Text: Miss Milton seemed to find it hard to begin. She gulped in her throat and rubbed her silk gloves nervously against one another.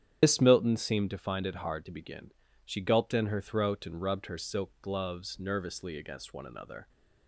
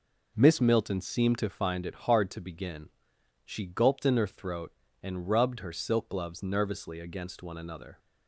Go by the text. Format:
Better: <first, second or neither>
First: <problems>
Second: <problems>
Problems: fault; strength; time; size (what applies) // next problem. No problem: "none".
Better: second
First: loses the start of "Miss"; at 0.2 s; 120 ms // starts louder than the rest; strong; until 1.2 s; 9 dB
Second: none